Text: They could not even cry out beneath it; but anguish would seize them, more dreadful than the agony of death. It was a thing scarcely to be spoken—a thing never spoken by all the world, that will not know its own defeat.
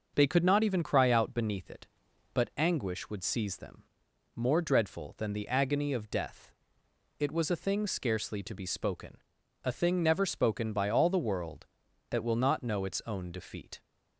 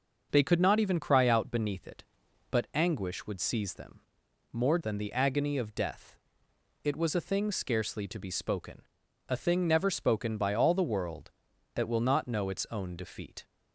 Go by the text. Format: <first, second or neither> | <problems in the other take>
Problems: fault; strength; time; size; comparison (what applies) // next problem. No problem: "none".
first | starts louder than the rest; noticeable; until 1.3 s; 6 dB; also in the first // skips "dreadful"; at 4.8 s